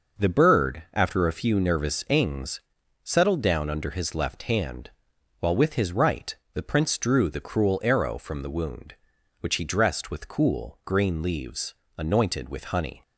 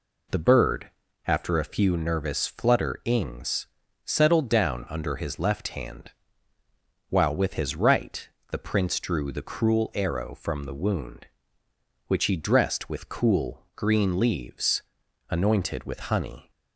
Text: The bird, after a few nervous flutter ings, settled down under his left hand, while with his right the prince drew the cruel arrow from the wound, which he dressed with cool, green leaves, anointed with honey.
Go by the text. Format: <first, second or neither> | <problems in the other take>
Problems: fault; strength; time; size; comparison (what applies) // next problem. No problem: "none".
second | skips "flutter"; at 2.0 s // pauses between "right" and "the"; slight; at 6.3 s; 0.20 s long; slight in the second